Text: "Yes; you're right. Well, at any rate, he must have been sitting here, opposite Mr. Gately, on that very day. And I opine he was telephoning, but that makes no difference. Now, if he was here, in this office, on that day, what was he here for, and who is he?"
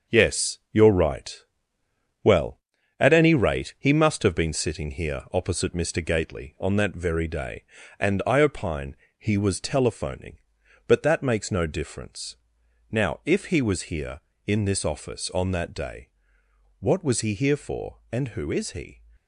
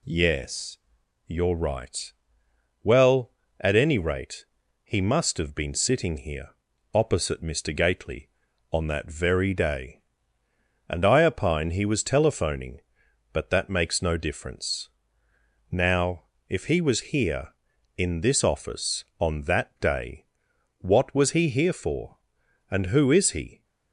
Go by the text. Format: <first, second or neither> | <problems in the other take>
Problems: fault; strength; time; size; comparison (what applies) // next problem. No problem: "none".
second | gets quieter; strong; throughout; 7.5 dB // pauses between "opine" and "he"; slight; at 8.9 s; 0.22 s long